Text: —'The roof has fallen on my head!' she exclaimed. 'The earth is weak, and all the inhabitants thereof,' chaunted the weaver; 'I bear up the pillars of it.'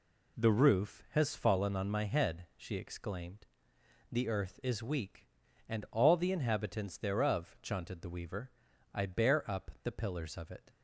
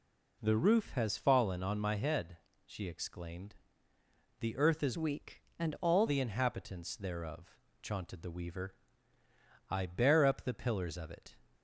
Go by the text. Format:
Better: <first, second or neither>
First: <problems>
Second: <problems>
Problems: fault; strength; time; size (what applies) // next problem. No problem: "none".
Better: first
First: none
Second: changes voice from "weak" to "all"; from 4.9 to 6.0 s; 1.1 s long